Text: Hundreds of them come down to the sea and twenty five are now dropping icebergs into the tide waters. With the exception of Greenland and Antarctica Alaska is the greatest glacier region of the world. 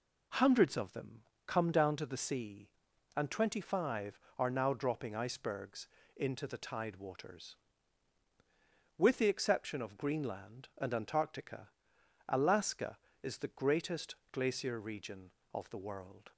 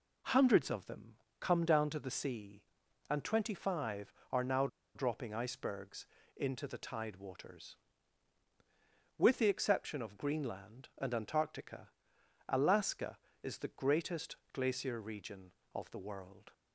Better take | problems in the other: first | pauses between "them" and "come"; slight; at 1.1 s; 0.24 s long; slight in the first // pauses between "now" and "dropping"; slight; at 4.6 s; 0.27 s long // pauses between "icebergs" and "into"; slight; at 6.0 s; 0.30 s long; slight in the first // pauses between "Antarctica" and "Alaska"; noticeable; at 11.8 s; 0.60 s long; noticeable in the first // pauses between "greatest" and "glacier"; slight; at 14.3 s; 0.16 s long; slight in the first

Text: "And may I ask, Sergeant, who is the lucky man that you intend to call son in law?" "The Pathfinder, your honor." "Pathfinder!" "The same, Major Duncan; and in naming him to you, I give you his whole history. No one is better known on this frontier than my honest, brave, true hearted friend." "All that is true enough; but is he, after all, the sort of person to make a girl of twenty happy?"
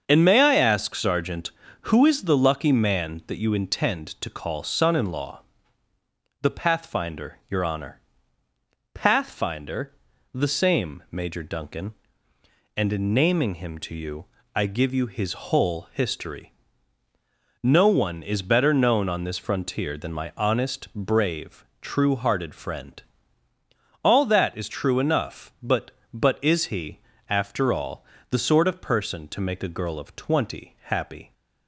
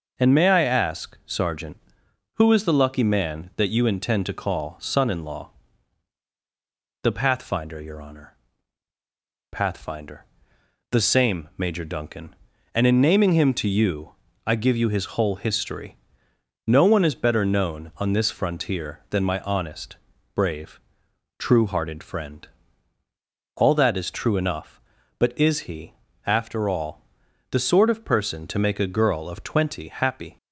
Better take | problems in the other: second | starts louder than the rest; until 1.0 s; 6.5 dB // says "but" twice; at 26.1 s

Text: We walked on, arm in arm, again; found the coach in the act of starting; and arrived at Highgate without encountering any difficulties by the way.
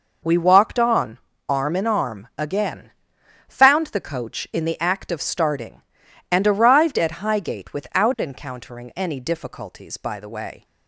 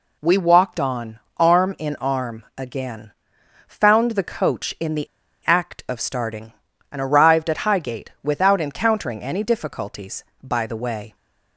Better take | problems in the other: first | pauses between "the" and "act"; at 5.0 s; 0.41 s long

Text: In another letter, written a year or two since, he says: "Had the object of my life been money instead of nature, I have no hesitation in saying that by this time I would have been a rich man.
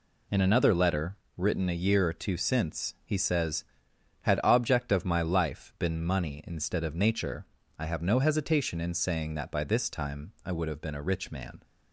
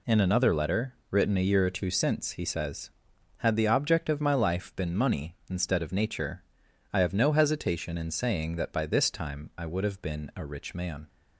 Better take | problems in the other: second | skips "the"; at 4.4 s

